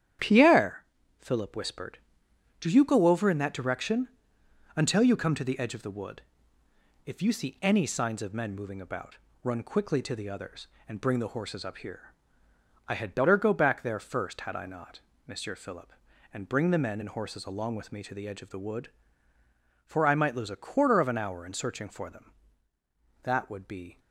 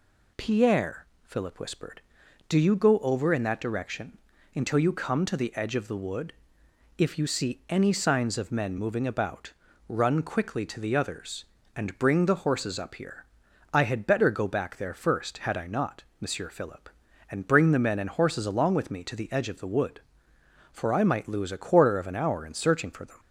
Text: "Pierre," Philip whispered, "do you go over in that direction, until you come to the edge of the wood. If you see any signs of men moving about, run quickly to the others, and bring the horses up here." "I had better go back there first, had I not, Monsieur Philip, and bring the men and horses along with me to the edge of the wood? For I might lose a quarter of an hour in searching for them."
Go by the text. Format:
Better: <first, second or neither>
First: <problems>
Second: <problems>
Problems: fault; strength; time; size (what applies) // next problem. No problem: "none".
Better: second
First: starts louder than the rest; strong; until 1.5 s; 10 dB // goes on to say "That would be"; noticeable; from 23.2 s on; 0.76 s long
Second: none